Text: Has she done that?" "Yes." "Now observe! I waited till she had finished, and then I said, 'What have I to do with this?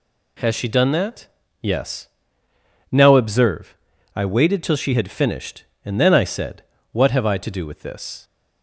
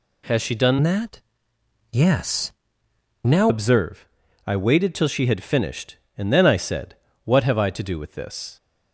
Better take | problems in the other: first | changes voice from "that" to "Now"; from 0.8 to 3.5 s; 2.7 s long

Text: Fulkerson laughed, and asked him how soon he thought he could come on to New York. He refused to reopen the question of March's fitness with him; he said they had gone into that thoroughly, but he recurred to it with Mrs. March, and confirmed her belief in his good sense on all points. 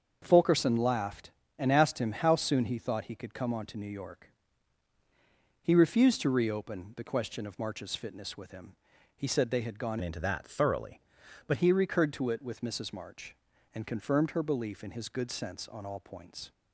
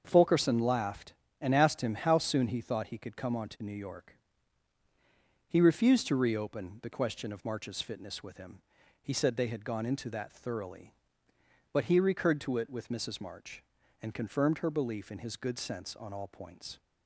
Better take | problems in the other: second | starts louder than the rest; until 1.2 s; 7 dB; also in the second // changes voice from "into" to "but"; from 10.0 to 11.5 s; 1.5 s long

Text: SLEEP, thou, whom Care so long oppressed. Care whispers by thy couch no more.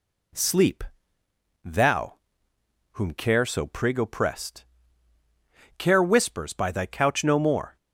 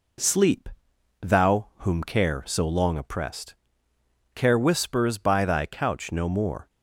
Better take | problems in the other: second | says "prig" for "long"; at 3.6 s

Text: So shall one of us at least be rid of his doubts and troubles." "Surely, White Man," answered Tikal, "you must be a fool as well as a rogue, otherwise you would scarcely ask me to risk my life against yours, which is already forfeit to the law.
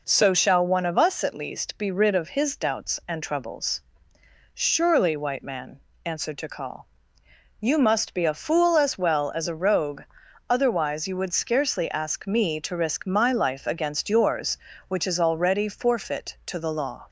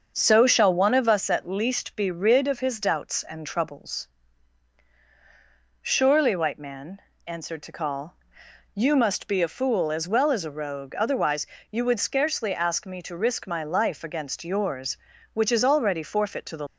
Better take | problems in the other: first | starts louder than the rest; until 1.1 s; 6.5 dB // pauses between "otherwise" and "you"; slight; at 11.4 s; 0.24 s long // stops before "law"; at 16.6 s

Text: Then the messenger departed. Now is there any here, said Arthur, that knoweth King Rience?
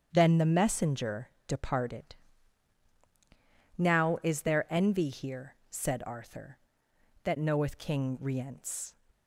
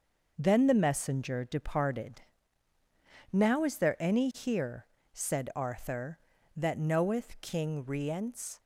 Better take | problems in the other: second | starts louder than the rest; strong; until 1.1 s; 8.5 dB // pauses between "messenger" and "departed"; slight; at 1.2 s; 0.18 s long // says "envy" for "any"; at 4.6 s

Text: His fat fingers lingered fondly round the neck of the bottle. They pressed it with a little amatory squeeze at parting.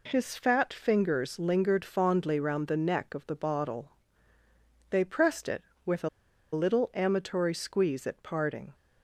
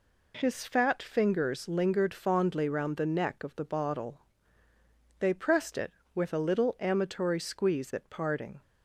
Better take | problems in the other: second | pauses between "a" and "little"; at 6.0 s; 0.44 s long

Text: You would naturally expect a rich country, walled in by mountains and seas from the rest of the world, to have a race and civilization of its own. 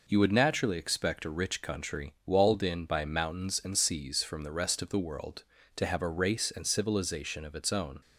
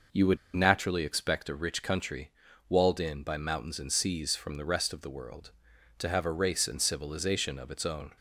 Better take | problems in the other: first | pauses between "would" and "naturally"; slight; at 0.3 s; 0.18 s long

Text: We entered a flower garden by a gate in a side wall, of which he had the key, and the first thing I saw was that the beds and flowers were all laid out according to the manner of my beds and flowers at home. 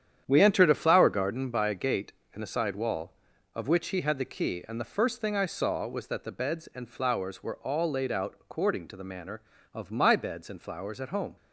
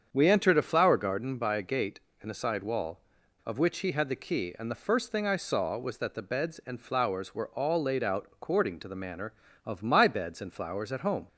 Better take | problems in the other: second | gets quieter; strong; throughout; 9 dB // starts louder than the rest; strong; until 1.2 s; 9 dB; strong in the second

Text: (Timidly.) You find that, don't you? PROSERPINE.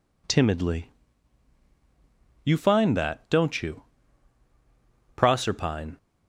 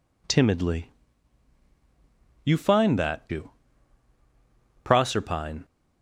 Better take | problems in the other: first | skips "don't"; at 3.2 s

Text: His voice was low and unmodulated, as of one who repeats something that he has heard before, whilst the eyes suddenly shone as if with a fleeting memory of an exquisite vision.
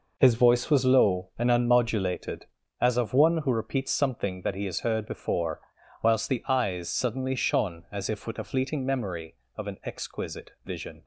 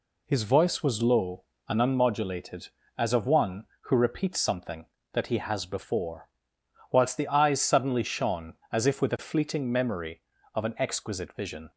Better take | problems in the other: first | skips "heard"; at 5.6 s

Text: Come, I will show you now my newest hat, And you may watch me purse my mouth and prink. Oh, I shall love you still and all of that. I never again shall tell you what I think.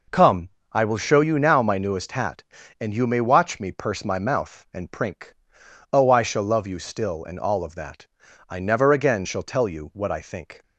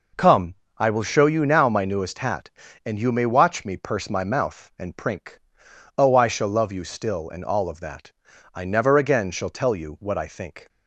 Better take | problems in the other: neither | none

